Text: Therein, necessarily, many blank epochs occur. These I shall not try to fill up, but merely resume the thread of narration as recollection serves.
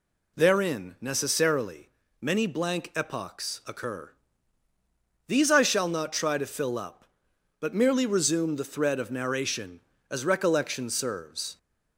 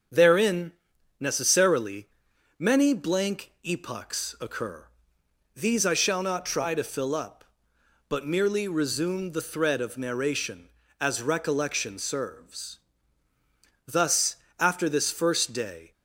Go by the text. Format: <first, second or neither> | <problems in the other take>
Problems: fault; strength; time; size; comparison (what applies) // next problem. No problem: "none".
first | starts louder than the rest; until 1.6 s; 7 dB // goes on to say "Thus after this first day"; strong; from 13.8 s on; 2.0 s long